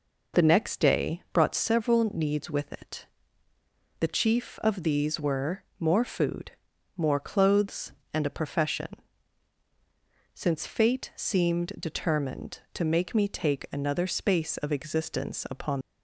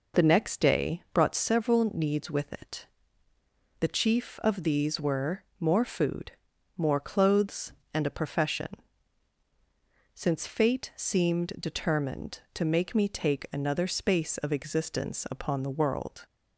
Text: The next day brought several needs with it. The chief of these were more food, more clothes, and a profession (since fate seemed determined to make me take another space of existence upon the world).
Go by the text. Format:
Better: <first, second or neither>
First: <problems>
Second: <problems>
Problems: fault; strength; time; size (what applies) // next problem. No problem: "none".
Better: second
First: pauses between "were" and "more"; slight; at 5.6 s; 0.16 s long // stops before "the world"; at 15.8 s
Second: pauses between "were" and "more"; slight; at 5.4 s; 0.16 s long